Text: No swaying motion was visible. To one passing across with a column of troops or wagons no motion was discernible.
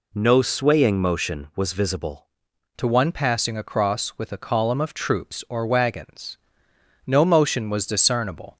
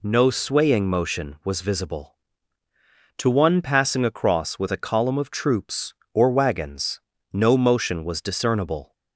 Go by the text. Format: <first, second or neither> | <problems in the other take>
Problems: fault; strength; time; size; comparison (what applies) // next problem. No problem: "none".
second | changes voice at "To"; from 2.7 s on; 5.8 s long // pauses between "wagons" and "no"; noticeable; at 6.3 s; 0.70 s long; slight in the second